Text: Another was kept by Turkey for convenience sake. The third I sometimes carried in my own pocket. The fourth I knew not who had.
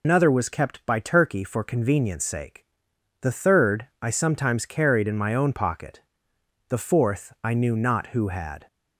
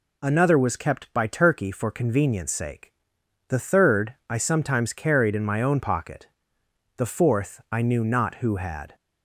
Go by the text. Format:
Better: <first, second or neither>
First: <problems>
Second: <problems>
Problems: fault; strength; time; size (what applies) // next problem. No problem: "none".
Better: second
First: loses the start of "Another"; at 0.0 s; 105 ms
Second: none